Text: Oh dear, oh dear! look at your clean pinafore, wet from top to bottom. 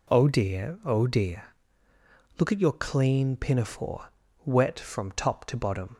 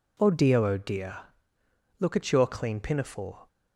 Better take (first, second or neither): first